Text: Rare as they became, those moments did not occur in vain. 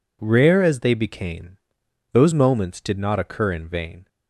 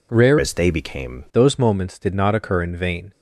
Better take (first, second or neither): first